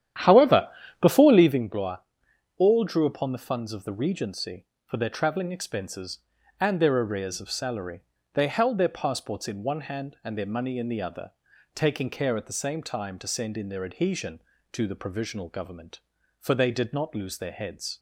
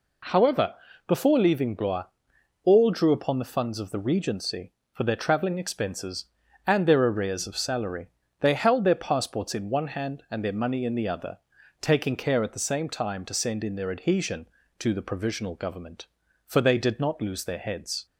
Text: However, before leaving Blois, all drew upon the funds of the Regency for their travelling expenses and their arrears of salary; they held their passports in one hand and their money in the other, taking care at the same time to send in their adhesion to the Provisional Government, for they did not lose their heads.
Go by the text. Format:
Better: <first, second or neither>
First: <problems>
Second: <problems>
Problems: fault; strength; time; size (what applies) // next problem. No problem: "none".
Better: second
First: starts louder than the rest; strong; until 1.7 s; 10.5 dB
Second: none